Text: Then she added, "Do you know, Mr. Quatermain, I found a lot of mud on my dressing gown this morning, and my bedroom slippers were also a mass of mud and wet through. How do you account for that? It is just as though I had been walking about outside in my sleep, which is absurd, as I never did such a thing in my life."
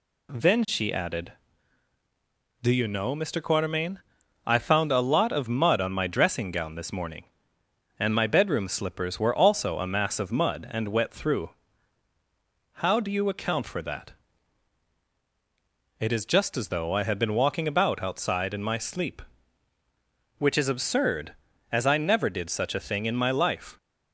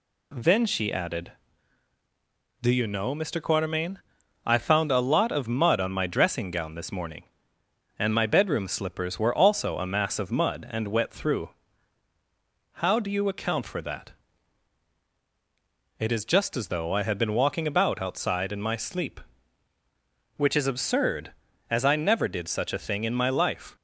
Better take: neither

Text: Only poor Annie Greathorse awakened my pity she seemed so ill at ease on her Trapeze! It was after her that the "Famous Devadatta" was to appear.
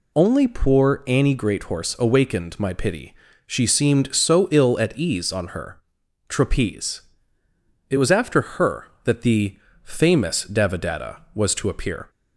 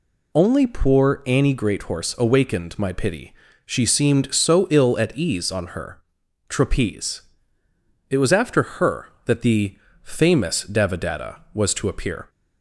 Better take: neither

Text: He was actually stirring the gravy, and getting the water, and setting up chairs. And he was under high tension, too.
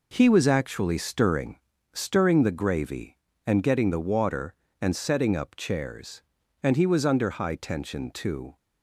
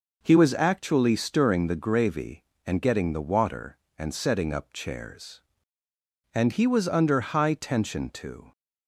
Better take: second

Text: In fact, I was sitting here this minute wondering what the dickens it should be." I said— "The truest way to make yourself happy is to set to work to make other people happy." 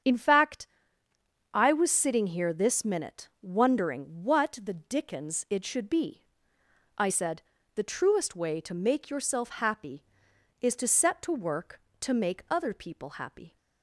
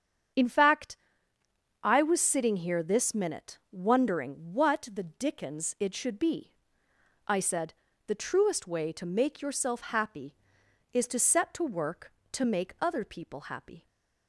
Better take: neither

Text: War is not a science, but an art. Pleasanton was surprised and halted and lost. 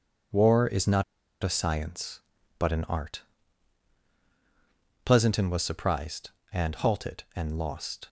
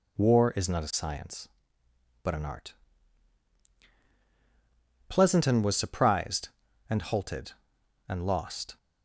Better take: second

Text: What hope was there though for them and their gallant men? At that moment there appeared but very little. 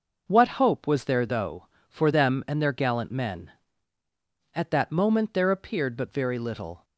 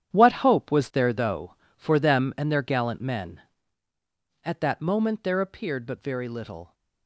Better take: first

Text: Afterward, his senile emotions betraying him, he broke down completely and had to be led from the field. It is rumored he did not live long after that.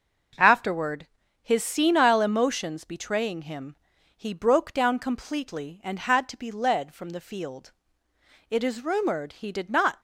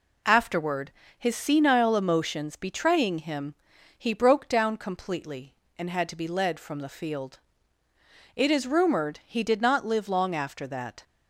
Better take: second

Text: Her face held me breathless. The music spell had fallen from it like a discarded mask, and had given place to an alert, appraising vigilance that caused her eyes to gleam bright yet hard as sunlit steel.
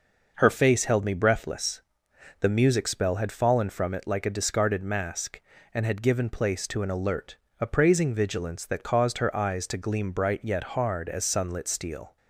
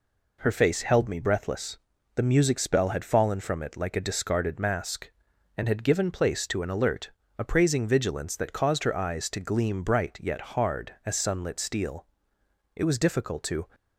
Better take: first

